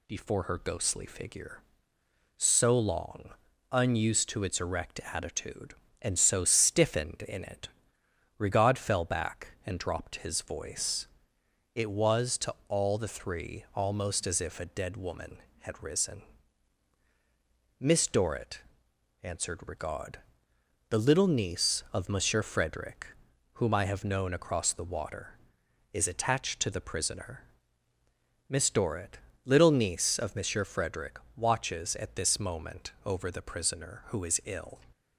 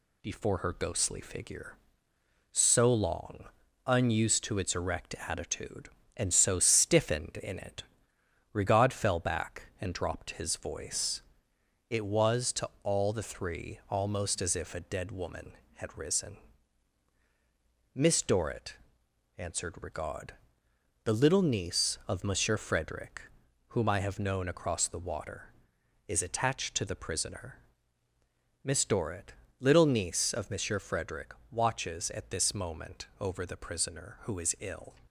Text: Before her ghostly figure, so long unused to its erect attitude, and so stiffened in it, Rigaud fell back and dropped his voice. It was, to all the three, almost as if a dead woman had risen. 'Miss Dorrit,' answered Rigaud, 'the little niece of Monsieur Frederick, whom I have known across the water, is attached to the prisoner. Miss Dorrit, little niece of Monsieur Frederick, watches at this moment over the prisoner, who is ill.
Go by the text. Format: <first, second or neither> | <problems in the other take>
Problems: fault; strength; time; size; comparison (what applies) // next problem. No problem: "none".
first | gets quieter; slight; throughout; 2.5 dB // pauses between "long" and "unused"; at 3.4 s; 0.40 s long; also in the first // pauses between "to" and "all"; slight; at 12.6 s; 0.16 s long; slight in the first